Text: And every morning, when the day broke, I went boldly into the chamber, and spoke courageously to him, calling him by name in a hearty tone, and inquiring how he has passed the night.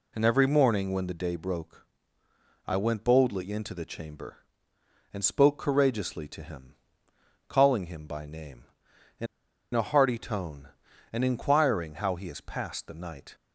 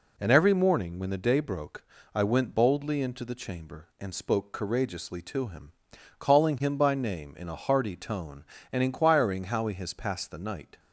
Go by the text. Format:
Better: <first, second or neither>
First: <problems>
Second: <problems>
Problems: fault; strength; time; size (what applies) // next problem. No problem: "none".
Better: second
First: pauses between "in" and "a"; noticeable; at 9.2 s; 0.48 s long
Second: none